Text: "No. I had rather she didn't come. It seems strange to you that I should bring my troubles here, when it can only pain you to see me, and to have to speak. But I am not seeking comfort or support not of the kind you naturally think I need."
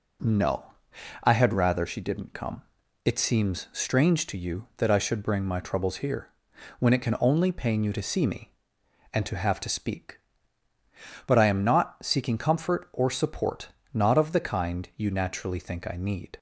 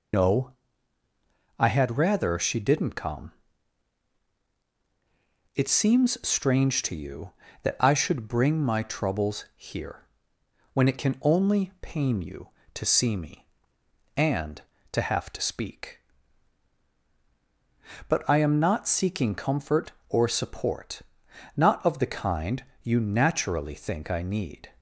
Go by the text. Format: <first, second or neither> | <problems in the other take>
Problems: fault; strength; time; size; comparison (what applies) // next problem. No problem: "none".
first | loses the start of "No"; at 0.1 s; 70 ms // pauses between "support" and "not"; noticeable; at 21.0 s; 0.54 s long; slight in the first // pauses between "kind" and "you"; slight; at 22.6 s; 0.18 s long